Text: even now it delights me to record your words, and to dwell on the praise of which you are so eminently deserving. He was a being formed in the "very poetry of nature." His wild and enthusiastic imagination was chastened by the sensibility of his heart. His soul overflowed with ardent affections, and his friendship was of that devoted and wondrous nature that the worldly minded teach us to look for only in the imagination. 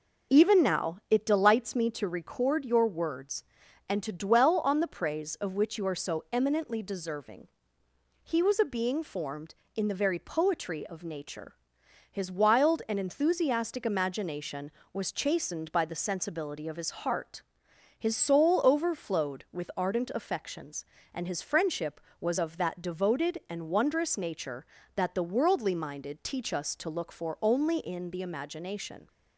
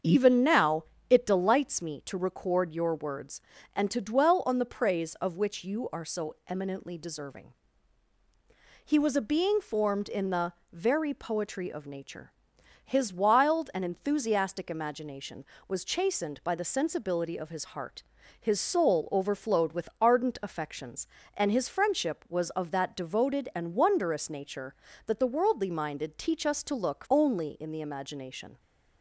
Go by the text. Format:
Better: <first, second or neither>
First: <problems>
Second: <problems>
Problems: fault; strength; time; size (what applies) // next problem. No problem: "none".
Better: first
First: none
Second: starts louder than the rest; until 1.2 s; 7 dB // pauses between "now" and "it"; slight; at 0.8 s; 0.24 s long // pauses between "the" and "very"; slight; at 10.5 s; 0.20 s long // skips "for"; at 27.0 s